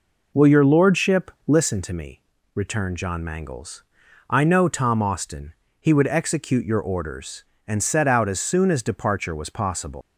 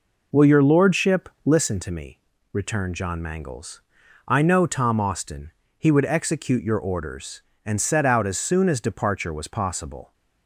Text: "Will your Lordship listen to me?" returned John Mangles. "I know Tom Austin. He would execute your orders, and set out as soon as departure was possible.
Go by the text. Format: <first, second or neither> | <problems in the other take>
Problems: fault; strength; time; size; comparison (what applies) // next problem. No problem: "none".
second | pauses between "Lordship" and "listen"; slight; at 1.3 s; 0.16 s long; slight in the second // leaves "possible" unfinished; at 10.0 s; 140 ms